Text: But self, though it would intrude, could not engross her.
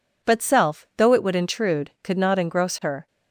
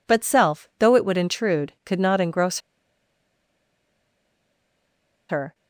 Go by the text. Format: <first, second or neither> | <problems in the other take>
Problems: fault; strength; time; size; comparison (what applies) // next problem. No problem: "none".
first | pauses between "engross" and "her"; strong; at 2.5 s; 2.7 s long